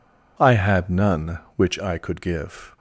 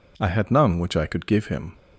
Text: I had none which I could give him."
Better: second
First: stops before "him"; at 2.7 s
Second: none

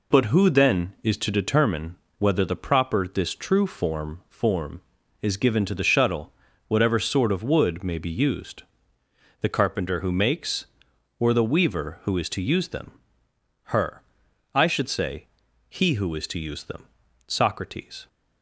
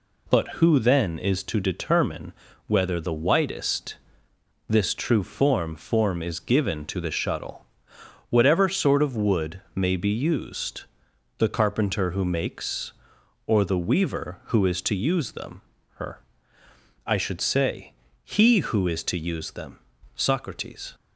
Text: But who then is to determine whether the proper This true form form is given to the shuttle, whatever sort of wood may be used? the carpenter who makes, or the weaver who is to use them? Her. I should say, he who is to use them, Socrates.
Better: first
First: pauses between "determine" and "whether"; slight; at 1.9 s; 0.22 s long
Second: pauses between "determine" and "whether"; slight; at 2.3 s; 0.34 s long // says "whitest" for "proper"; at 3.1 s

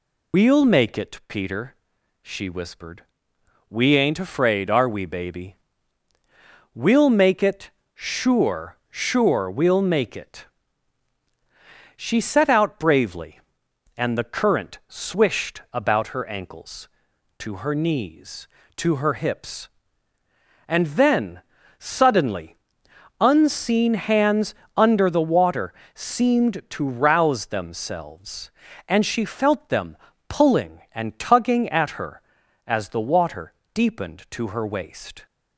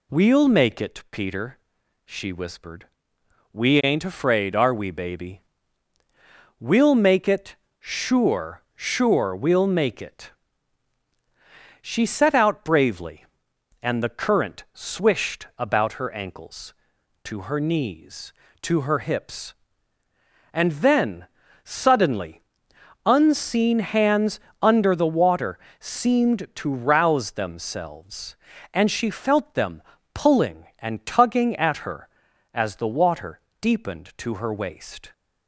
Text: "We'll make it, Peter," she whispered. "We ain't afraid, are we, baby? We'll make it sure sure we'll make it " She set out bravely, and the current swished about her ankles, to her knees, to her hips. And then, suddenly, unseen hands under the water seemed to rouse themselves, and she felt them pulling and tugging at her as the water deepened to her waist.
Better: second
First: loses the start of "We'll"; at 0.3 s; 70 ms // pauses between "it" and "sure"; slight; at 7.6 s; 0.26 s long // pauses between "hands" and "under"; slight; at 24.5 s; 0.22 s long // pauses between "water" and "seemed"; slight; at 25.7 s; 0.24 s long // pauses between "them" and "pulling"; slight; at 29.9 s; 0.34 s long // pauses between "water" and "deepened"; slight; at 33.5 s; 0.20 s long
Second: pauses between "it" and "sure"; slight; at 7.5 s; 0.26 s long // pauses between "hands" and "under"; slight; at 24.3 s; 0.22 s long // pauses between "water" and "seemed"; slight; at 25.5 s; 0.24 s long // pauses between "them" and "pulling"; slight; at 29.8 s; 0.34 s long // pauses between "water" and "deepened"; slight; at 33.4 s; 0.20 s long

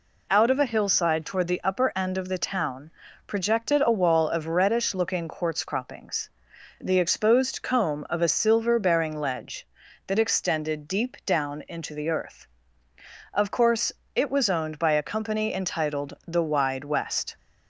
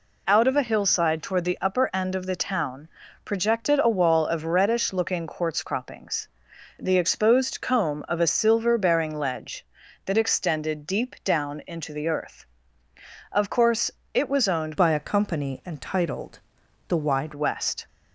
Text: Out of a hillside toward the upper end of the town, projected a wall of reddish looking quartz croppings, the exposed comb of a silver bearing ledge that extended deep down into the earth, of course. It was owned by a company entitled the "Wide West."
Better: first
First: none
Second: changes voice from "by" to "Wide"; from 14.7 to 17.3 s; 2.6 s long // pauses between "entitled" and "the"; noticeable; at 16.3 s; 0.50 s long

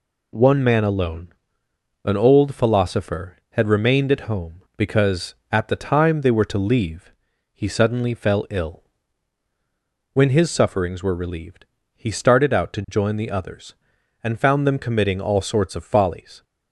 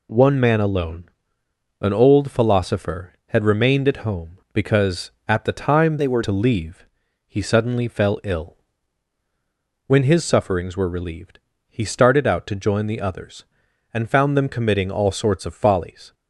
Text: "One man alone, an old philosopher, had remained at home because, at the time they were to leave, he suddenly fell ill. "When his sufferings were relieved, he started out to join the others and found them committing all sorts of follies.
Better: first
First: none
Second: changes voice from "they" to "were"; from 5.9 to 6.2 s; 0.3 s long

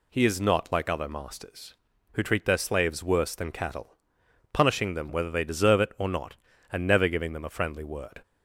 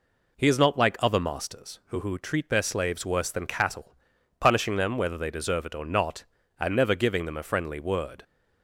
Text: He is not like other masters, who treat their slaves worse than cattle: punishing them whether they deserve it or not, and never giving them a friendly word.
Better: first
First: none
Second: says "who" twice; at 2.0 s

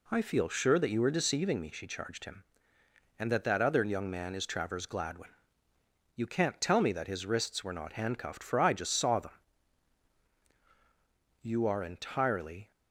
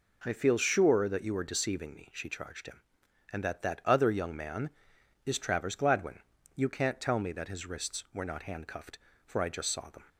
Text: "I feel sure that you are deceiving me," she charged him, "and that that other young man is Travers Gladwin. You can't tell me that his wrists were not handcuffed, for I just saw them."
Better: second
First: goes on to say "You are entirely"; noticeable; from 11.4 s on; 1.2 s long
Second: none

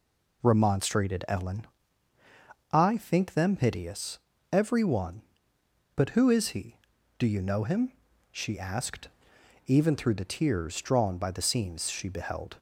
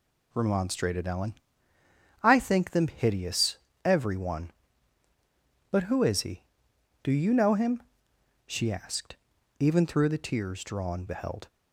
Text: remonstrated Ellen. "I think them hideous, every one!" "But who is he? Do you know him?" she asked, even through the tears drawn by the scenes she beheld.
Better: first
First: none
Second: skips "by the scenes she"; at 11.0 s

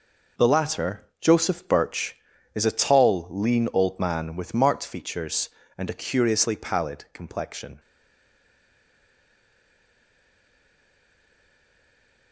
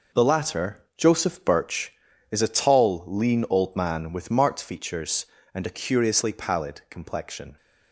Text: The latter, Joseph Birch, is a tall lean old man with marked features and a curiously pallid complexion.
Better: second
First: stays silent after the last word; strong; from 7.7 s on; 4.6 s long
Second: none

